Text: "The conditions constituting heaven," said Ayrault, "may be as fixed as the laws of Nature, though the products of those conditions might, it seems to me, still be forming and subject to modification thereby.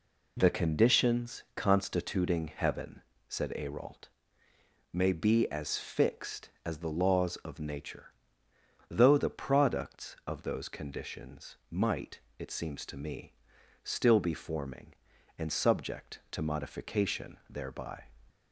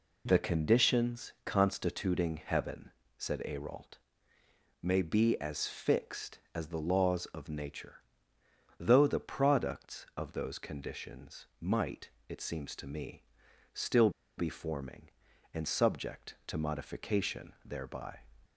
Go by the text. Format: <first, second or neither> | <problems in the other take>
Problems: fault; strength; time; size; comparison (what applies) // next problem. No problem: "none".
first | pauses between "still" and "be"; slight; at 14.1 s; 0.27 s long